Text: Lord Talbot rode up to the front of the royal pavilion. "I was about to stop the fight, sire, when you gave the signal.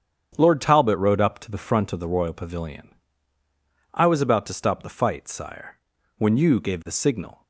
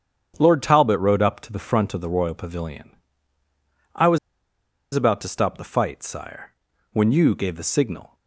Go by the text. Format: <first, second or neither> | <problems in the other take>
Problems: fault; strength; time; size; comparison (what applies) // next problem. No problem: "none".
first | starts louder than the rest; strong; until 1.3 s; 8.5 dB; strong in the first // pauses between "was" and "about"; noticeable; at 4.1 s; 0.75 s long